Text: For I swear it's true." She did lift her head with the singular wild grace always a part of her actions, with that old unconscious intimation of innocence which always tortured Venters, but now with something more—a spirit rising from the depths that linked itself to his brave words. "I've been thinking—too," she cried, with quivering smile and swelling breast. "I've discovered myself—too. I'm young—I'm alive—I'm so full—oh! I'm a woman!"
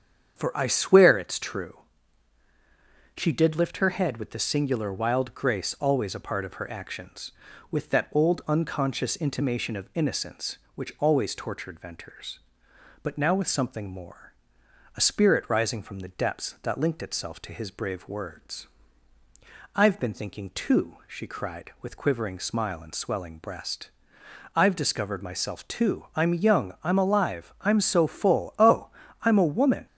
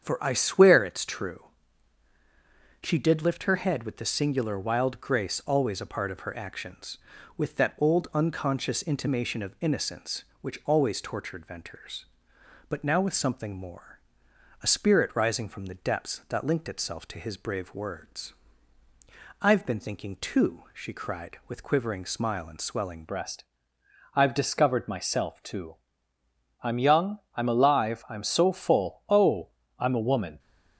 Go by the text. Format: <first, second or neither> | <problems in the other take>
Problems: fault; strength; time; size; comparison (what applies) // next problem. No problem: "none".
first | starts louder than the rest; strong; until 1.0 s; 8 dB; strong in the first // changes voice at "breast"; from 23.0 s on; 7.3 s long